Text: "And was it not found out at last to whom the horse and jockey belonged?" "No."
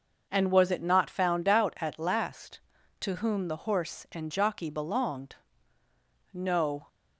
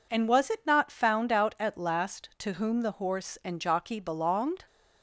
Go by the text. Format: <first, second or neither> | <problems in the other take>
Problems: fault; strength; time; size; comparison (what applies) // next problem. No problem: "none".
first | stops before "No"; at 4.6 s